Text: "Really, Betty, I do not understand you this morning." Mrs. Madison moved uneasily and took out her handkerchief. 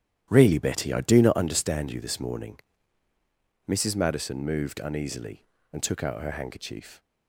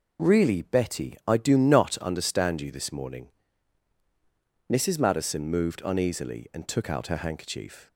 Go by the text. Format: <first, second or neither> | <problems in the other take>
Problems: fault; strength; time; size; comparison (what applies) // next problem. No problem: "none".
second | starts louder than the rest; strong; until 1.7 s; 11 dB